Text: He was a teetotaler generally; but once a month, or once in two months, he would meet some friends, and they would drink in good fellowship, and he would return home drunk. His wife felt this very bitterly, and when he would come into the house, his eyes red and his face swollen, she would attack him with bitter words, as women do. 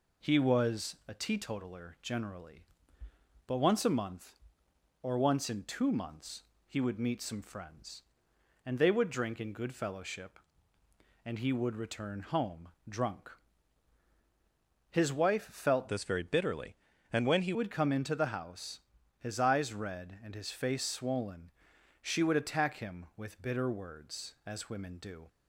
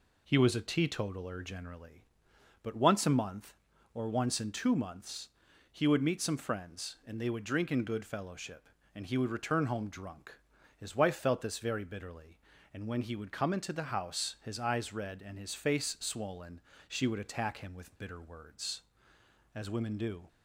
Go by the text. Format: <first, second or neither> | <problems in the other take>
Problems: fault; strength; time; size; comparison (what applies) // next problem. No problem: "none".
second | pauses between "home" and "drunk"; slight; at 12.6 s; 0.18 s long // changes voice from "this" to "he"; from 15.8 to 17.5 s; 1.7 s long